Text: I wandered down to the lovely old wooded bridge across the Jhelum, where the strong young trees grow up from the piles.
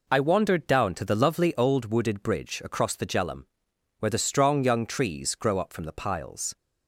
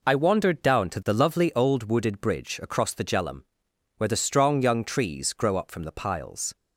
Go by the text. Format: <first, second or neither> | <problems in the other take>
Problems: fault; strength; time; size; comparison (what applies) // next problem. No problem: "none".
neither | none